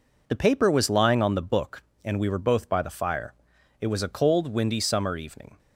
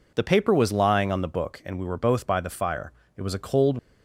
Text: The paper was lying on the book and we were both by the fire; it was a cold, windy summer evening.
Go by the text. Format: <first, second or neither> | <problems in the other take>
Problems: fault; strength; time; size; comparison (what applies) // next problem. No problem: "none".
first | stops before "windy summer evening"; at 3.7 s